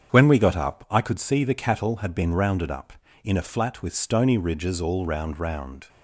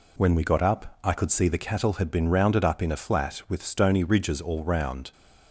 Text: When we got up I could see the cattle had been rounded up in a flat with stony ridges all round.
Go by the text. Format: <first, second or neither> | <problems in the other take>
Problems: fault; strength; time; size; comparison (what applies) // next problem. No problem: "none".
second | starts louder than the rest; strong; until 1.1 s; 8 dB // says "round" twice; at 5.3 s